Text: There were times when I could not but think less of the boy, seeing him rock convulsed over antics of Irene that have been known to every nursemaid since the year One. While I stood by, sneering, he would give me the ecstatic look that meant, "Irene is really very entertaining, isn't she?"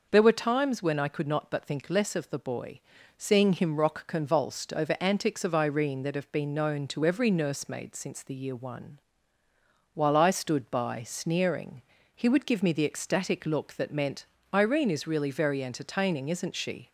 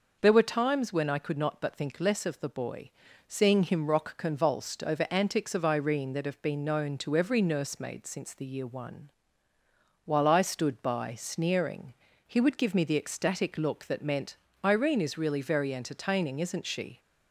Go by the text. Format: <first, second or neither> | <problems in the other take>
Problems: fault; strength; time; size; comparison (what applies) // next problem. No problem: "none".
neither | none